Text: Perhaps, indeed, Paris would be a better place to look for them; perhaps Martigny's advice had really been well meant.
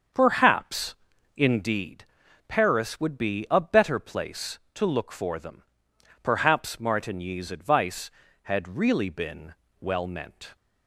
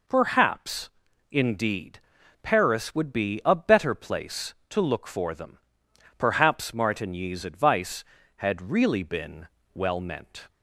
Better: second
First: starts louder than the rest; until 1.7 s; 7 dB // pauses between "been" and "well"; slight; at 9.5 s; 0.28 s long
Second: pauses between "been" and "well"; slight; at 9.4 s; 0.28 s long

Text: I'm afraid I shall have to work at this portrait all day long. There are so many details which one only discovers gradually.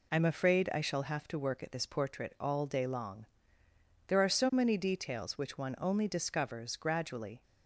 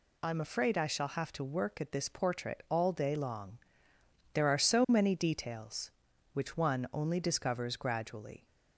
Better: neither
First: none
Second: none

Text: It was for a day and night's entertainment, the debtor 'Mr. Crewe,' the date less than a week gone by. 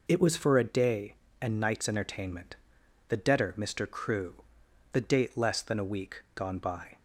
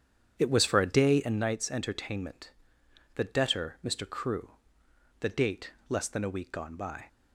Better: first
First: none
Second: starts louder than the rest; strong; until 1.5 s; 8.5 dB // pauses between "date" and "less"; slight; at 5.7 s; 0.18 s long

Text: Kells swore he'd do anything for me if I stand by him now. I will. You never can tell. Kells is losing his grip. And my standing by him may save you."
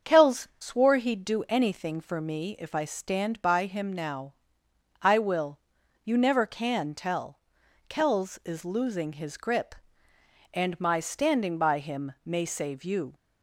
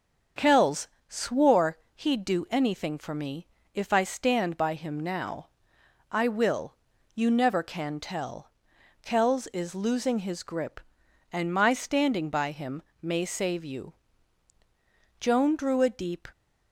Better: first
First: starts louder than the rest; until 1.1 s; 7 dB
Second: starts louder than the rest; until 1.5 s; 7 dB // pauses between "Kells" and "swore"; slight; at 0.8 s; 0.22 s long // pauses between "swore" and "he'd"; slight; at 1.7 s; 0.16 s long // pauses between "me" and "if"; slight; at 3.4 s; 0.26 s long // pauses between "him" and "may"; slight; at 12.8 s; 0.20 s long // goes on to say "Joan drew a deep"; noticeable; from 15.1 s on; 1.1 s long

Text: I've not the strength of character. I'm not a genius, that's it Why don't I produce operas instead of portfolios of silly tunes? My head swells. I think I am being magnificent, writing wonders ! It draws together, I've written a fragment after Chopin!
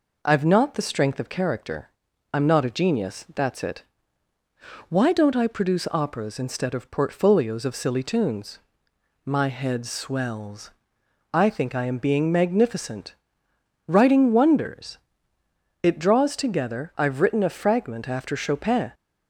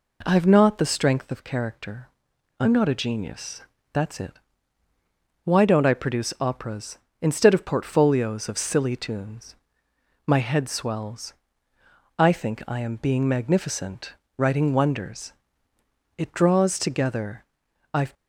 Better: first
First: pauses between "it" and "Why"; at 3.8 s; 1.0 s long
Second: pauses between "it" and "Why"; at 4.3 s; 1.1 s long // stops before "written a fragment after Chopin"; at 18.1 s

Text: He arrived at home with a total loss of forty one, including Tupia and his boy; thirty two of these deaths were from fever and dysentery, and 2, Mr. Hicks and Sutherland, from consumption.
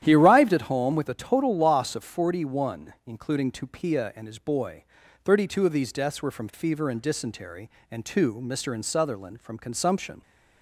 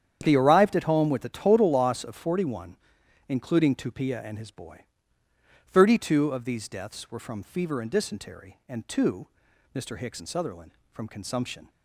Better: second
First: starts louder than the rest; strong; until 1.0 s; 11 dB // skips "Hicks"; at 8.7 s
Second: starts louder than the rest; strong; until 1.2 s; 9 dB

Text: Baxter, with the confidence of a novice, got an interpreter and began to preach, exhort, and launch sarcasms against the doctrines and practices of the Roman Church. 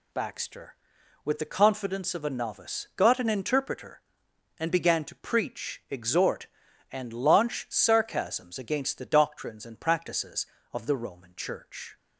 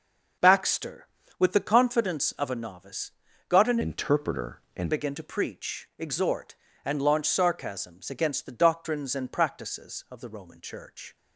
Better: first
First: none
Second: changes voice from "interpreter" to "and"; from 3.8 to 4.9 s; 1.1 s long

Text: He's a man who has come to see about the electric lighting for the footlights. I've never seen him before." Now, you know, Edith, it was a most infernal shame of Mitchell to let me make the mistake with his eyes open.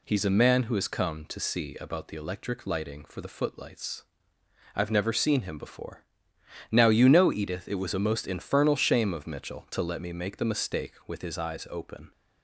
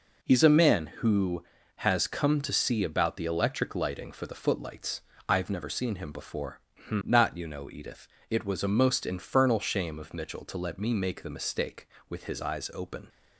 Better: first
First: none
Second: says "Not" for "Now"; at 6.8 s

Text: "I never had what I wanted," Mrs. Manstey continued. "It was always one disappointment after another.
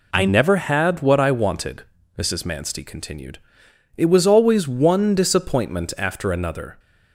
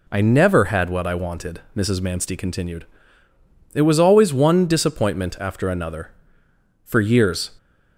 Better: first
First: none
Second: goes on to say "For years"; noticeable; from 6.8 s on; 0.64 s long

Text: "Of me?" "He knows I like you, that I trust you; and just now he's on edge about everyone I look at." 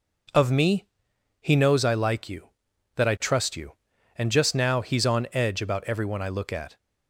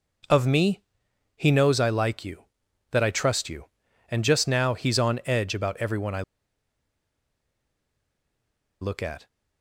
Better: first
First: none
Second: pauses between "I" and "look"; strong; at 6.2 s; 2.5 s long

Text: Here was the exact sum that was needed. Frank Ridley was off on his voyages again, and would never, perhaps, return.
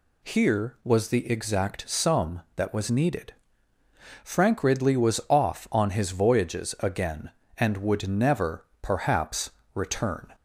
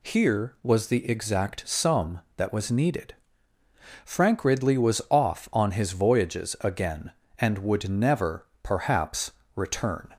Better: neither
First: none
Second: none

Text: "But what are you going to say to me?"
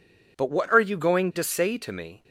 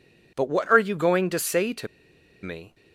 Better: first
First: none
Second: pauses between "to" and "me"; noticeable; at 1.8 s; 0.55 s long

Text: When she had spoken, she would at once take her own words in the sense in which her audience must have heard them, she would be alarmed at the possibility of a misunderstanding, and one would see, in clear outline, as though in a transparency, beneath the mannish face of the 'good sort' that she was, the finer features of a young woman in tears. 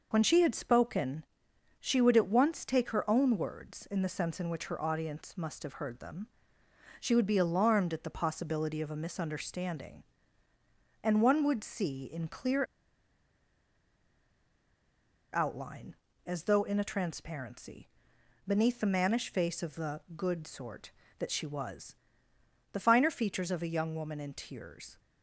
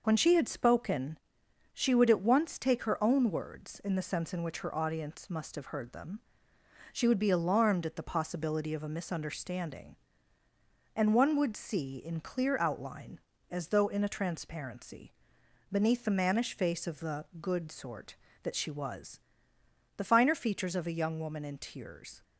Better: second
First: pauses between "clear" and "outline"; strong; at 12.6 s; 2.6 s long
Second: none

